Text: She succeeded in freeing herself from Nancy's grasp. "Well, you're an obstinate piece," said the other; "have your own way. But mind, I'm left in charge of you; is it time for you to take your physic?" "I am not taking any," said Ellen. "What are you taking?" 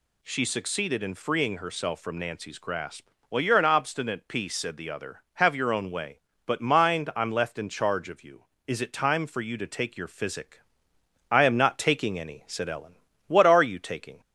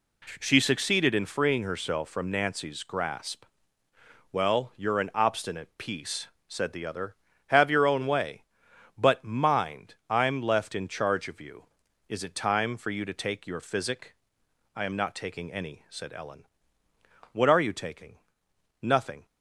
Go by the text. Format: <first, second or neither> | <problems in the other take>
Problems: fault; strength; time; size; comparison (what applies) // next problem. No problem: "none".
first | goes on to say "Nothing"; slight; from 18.8 s on; 0.44 s long